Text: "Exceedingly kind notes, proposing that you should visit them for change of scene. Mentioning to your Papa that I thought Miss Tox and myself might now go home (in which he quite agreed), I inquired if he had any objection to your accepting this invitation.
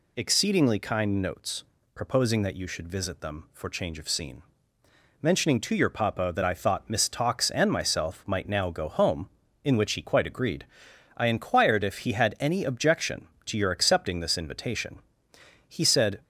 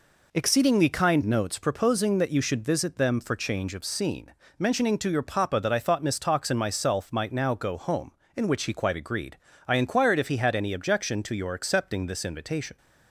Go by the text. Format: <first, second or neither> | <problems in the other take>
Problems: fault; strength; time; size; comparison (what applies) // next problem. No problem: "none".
second | goes on to say "He said"; from 15.6 s on; 0.54 s long